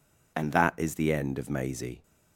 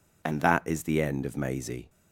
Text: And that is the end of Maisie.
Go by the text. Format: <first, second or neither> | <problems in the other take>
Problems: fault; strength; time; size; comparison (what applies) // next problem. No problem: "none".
neither | none